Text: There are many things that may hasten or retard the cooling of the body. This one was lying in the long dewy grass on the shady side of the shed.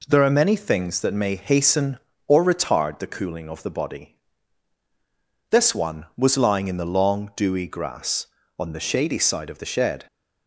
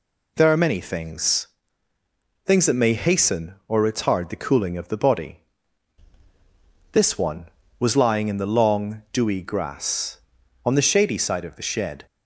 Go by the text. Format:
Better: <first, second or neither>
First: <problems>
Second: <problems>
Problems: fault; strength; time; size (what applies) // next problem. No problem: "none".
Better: first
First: none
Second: says "things" twice; at 2.4 s